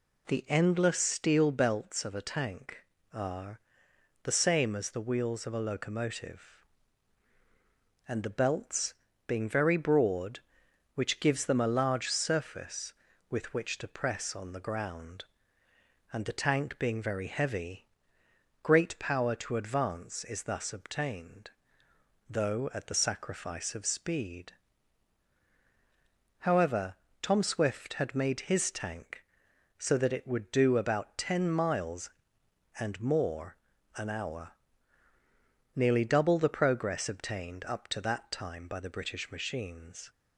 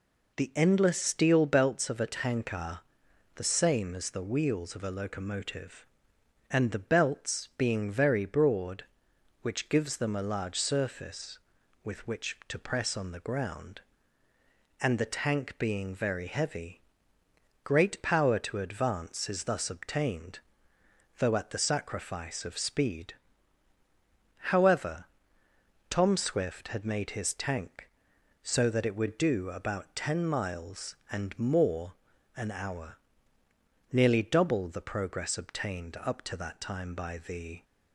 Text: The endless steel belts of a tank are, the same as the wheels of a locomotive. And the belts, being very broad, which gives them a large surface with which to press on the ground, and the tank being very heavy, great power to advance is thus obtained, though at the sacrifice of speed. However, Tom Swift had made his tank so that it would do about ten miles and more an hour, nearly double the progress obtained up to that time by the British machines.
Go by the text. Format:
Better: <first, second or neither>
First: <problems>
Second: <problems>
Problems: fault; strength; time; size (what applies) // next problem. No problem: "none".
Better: first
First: pauses between "more" and "an"; at 33.5 s; 0.40 s long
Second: pauses between "more" and "an"; at 31.9 s; 0.42 s long // stops before "British machines"; at 37.6 s